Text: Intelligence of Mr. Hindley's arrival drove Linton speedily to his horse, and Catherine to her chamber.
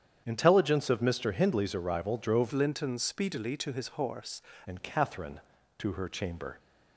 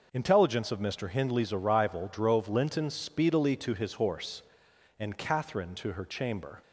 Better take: second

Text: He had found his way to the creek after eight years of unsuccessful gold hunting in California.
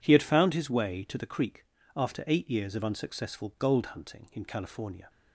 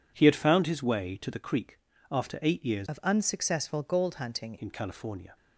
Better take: first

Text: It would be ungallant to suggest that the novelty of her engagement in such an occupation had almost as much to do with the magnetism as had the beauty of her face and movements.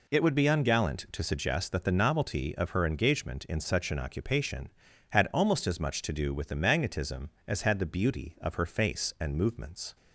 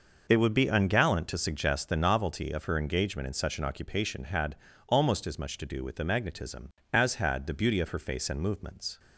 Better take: first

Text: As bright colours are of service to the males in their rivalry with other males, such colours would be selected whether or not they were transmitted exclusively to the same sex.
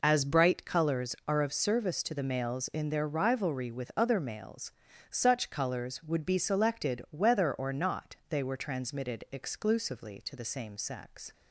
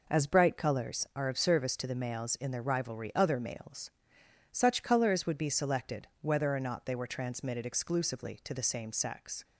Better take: first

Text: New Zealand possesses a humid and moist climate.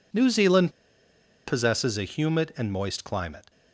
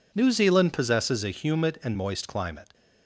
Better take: second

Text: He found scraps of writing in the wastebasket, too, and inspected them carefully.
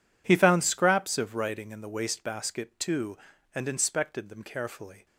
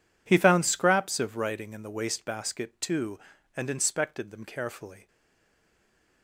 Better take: first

